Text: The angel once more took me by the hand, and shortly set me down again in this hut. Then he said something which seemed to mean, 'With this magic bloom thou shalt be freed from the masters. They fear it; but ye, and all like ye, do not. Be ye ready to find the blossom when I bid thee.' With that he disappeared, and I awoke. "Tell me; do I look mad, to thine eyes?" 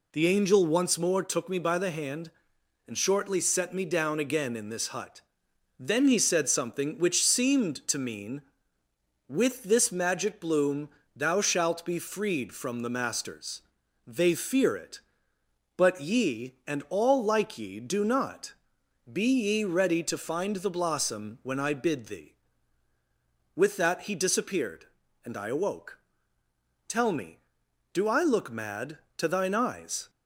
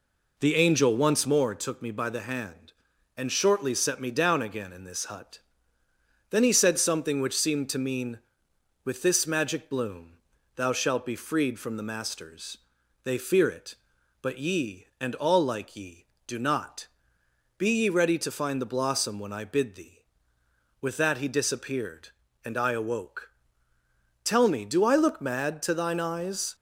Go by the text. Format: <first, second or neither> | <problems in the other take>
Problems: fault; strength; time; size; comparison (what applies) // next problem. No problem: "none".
first | starts louder than the rest; until 1.5 s; 3.5 dB // pauses between "bloom" and "thou"; at 10.1 s; 0.38 s long; slight in the first